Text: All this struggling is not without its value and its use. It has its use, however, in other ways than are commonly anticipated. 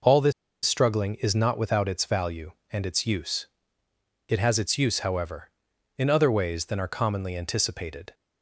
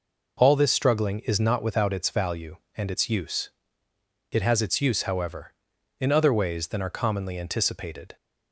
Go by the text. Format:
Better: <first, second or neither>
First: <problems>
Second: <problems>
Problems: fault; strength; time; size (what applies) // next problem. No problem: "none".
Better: second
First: pauses between "this" and "struggling"; slight; at 0.3 s; 0.33 s long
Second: none